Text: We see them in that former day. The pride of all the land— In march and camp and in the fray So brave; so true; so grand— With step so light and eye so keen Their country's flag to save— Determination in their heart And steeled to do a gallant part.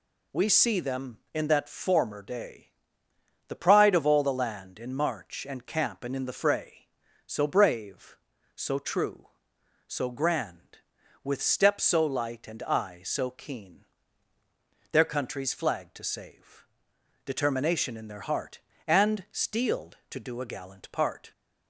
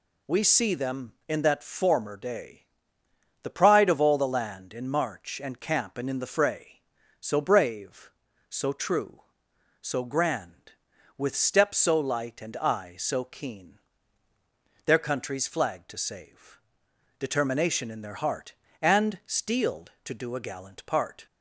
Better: neither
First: pauses between "keen" and "Their"; at 13.8 s; 1.0 s long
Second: pauses between "keen" and "Their"; at 13.7 s; 1.0 s long

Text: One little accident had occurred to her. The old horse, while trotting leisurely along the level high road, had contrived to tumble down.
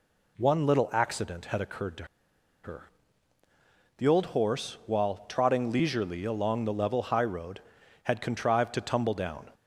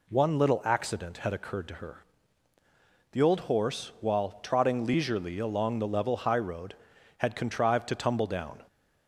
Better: second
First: pauses between "to" and "her"; noticeable; at 2.0 s; 0.59 s long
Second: none

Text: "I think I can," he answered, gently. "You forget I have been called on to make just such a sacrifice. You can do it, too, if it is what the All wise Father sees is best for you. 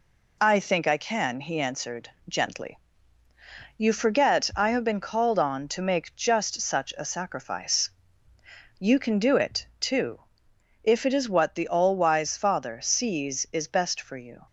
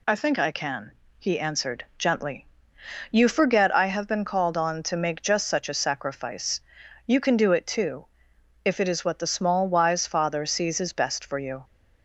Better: first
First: none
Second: says "Small" for "All"; at 9.3 s

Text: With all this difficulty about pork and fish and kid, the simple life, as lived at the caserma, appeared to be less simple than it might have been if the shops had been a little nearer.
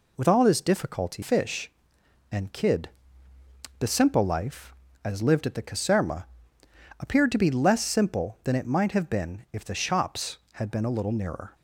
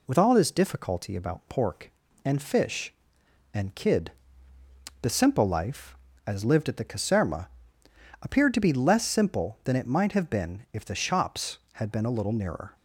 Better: second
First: skips "about pork and"; at 1.2 s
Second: none

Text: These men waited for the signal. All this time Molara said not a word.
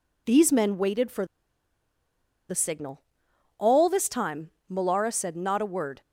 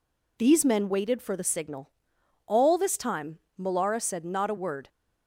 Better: second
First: pauses between "for" and "the"; at 1.2 s; 1.2 s long // pauses between "time" and "Molara"; slight; at 4.5 s; 0.20 s long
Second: pauses between "time" and "Molara"; slight; at 3.3 s; 0.20 s long

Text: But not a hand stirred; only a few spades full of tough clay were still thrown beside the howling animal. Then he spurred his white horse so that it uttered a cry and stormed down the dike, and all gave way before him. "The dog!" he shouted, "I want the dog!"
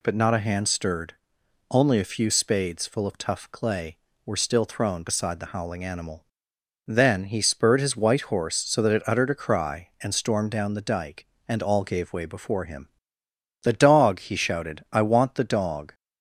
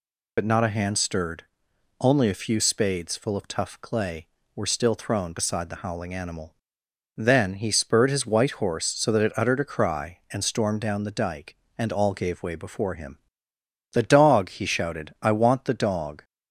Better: first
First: none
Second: loses the start of "But"; at 0.3 s; 60 ms

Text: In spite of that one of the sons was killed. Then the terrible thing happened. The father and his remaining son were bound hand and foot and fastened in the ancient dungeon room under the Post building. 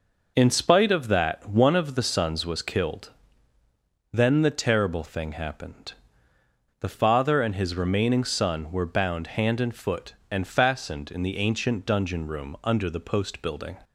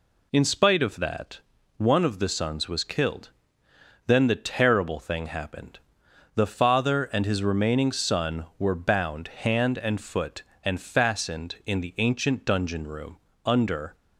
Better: first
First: none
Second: pauses between "that" and "one"; at 1.3 s; 0.38 s long // pauses between "room" and "under"; slight; at 13.1 s; 0.26 s long // stops before "the Post building"; at 13.9 s

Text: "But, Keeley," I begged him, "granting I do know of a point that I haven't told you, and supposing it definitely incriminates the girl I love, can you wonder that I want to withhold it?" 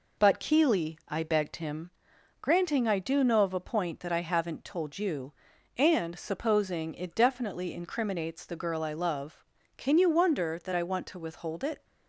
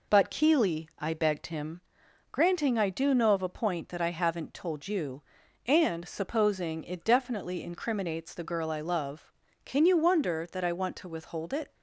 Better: neither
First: none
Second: none

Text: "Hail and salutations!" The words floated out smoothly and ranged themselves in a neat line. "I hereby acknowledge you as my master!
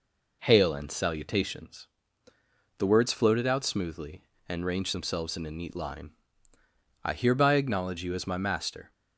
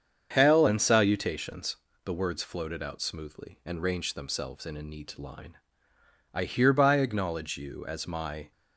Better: first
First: none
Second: starts louder than the rest; strong; until 1.3 s; 7.5 dB // stops before "master"; at 8.5 s

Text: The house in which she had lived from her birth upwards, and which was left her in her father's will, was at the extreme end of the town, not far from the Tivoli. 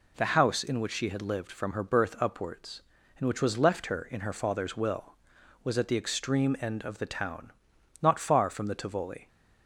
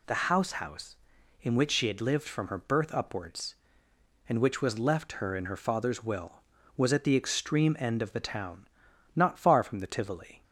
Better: first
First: none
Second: says "house" twice; at 0.6 s

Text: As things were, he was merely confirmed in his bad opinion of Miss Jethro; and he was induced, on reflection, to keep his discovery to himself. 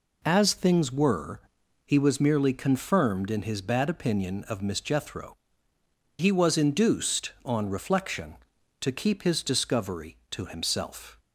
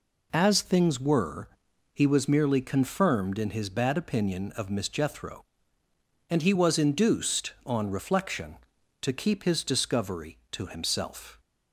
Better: second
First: skips "and"; at 5.7 s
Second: none

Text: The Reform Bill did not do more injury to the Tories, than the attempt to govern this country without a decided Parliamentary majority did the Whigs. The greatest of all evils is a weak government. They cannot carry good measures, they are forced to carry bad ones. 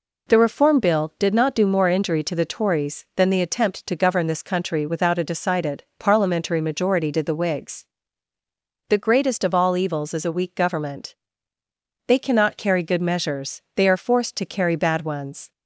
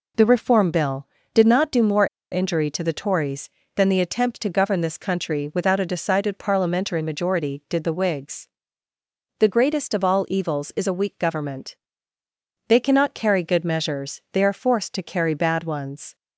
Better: first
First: none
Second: pauses between "more" and "injury"; slight; at 2.0 s; 0.24 s long

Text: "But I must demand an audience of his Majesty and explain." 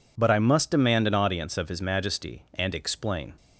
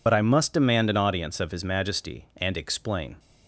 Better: first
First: none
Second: loses the start of "But"; at 0.0 s; 60 ms

